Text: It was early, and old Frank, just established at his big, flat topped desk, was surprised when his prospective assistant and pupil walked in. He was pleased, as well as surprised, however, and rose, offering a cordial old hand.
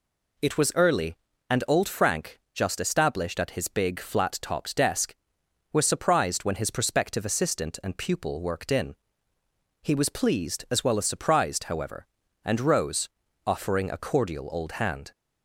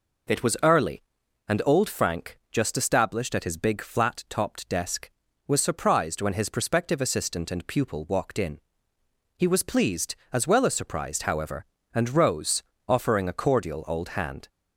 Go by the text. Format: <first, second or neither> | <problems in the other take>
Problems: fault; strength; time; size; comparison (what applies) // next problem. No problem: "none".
second | says "worked" for "walked"; at 8.4 s